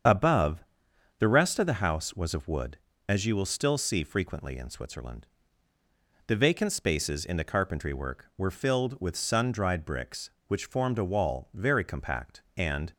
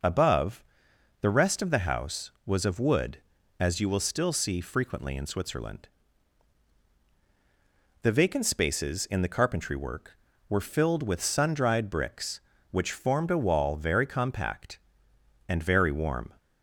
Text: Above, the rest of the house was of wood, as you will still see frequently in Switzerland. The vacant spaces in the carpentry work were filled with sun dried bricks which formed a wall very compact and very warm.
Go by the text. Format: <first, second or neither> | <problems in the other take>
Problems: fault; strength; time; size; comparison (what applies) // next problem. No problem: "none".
second | starts louder than the rest; strong; until 1.6 s; 7.5 dB // stops before "very warm"; at 12.9 s